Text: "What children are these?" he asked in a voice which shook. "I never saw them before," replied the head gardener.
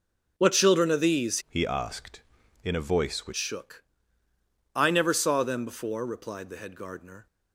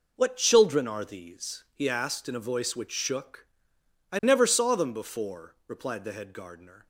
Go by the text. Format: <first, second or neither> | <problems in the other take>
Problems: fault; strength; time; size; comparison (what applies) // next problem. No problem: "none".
second | changes voice from "he" to "which"; from 1.4 to 3.3 s; 1.9 s long